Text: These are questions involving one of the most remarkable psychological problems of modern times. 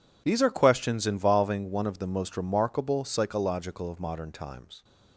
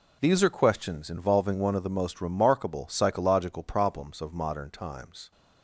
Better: second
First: skips "problems"; at 3.8 s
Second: none

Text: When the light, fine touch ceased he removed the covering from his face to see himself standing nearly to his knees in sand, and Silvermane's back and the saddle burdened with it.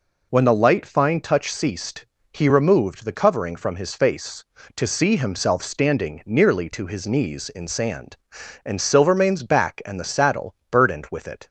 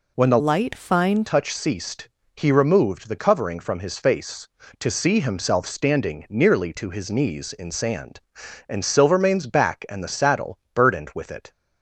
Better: first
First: pauses between "ceased" and "he"; slight; at 2.0 s; 0.30 s long // pauses between "saddle" and "burdened"; slight; at 10.5 s; 0.16 s long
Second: changes voice from "light" to "fine"; from 0.3 to 1.2 s; 0.9 s long // pauses between "ceased" and "he"; slight; at 2.0 s; 0.30 s long // pauses between "saddle" and "burdened"; slight; at 10.5 s; 0.16 s long

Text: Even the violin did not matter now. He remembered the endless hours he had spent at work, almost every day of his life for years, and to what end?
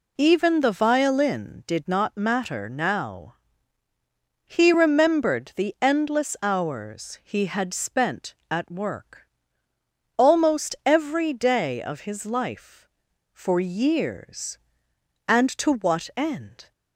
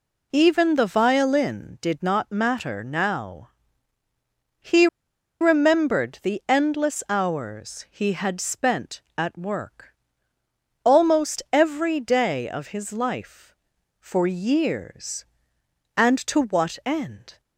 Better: first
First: none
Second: pauses between "He" and "remembered"; noticeable; at 4.8 s; 0.54 s long

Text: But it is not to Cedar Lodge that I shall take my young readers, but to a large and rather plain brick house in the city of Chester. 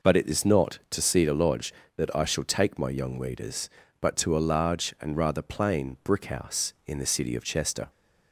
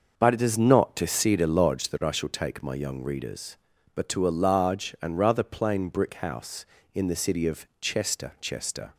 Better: first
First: none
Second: says "Chester" twice; at 8.4 s

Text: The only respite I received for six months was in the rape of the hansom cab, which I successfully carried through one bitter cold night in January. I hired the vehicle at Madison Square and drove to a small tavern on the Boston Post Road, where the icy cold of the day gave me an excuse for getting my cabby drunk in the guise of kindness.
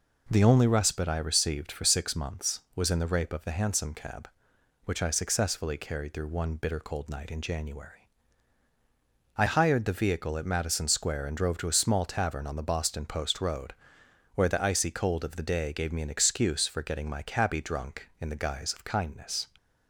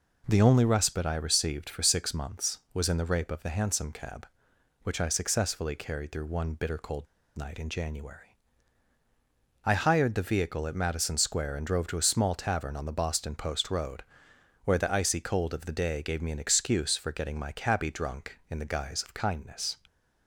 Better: first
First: none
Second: pauses between "cold" and "night"; slight; at 7.0 s; 0.31 s long

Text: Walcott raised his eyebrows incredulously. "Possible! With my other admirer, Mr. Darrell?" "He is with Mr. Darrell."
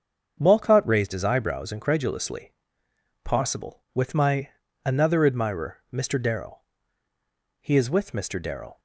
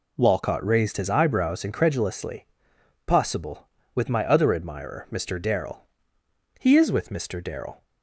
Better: second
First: starts louder than the rest; until 1.4 s; 7 dB // says "another" for "other"; at 4.8 s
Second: none

